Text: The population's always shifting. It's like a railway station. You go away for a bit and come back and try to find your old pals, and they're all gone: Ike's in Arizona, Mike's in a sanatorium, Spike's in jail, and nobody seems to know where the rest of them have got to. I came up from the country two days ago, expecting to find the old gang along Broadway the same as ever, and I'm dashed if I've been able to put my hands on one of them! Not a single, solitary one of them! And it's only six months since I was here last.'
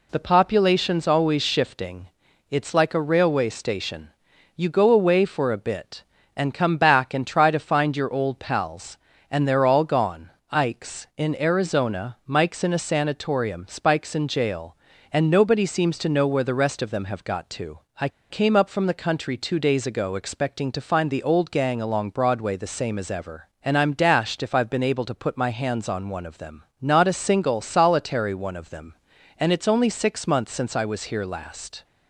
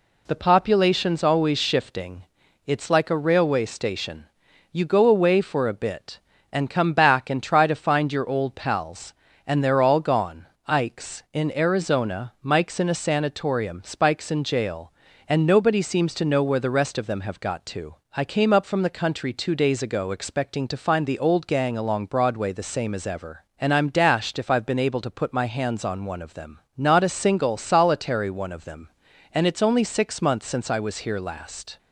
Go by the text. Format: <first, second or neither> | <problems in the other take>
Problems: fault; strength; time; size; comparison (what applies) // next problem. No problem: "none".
second | pauses between "I" and "came"; slight; at 18.0 s; 0.21 s long